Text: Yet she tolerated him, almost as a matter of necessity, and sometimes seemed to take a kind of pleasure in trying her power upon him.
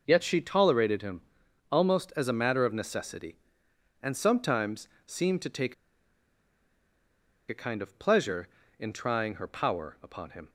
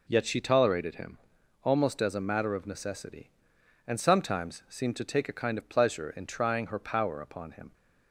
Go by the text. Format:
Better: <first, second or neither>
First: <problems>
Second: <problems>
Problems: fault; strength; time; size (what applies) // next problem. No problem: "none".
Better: second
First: pauses between "sometimes" and "seemed"; slight; at 4.8 s; 0.18 s long // pauses between "take" and "a"; strong; at 5.7 s; 1.7 s long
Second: none